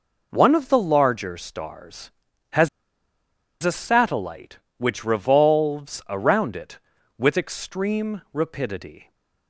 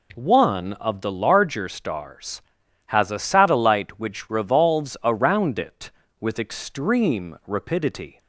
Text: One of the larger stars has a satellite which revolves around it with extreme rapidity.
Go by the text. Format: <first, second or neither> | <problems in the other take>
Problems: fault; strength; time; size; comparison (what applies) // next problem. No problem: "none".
second | pauses between "has" and "a"; noticeable; at 2.6 s; 0.94 s long